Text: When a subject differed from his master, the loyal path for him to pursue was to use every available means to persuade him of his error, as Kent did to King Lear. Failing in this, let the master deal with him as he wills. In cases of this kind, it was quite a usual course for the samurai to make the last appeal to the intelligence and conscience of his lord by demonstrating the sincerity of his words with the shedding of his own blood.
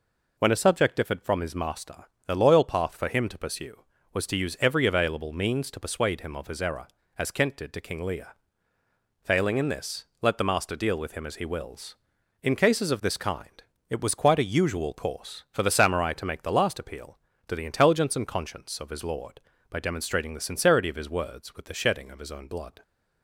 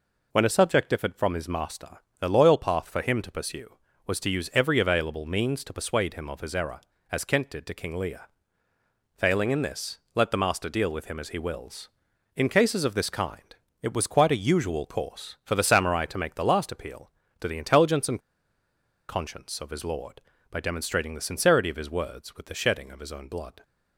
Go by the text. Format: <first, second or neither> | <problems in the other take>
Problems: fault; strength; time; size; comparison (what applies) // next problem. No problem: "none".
first | pauses between "and" and "conscience"; noticeable; at 18.1 s; 0.90 s long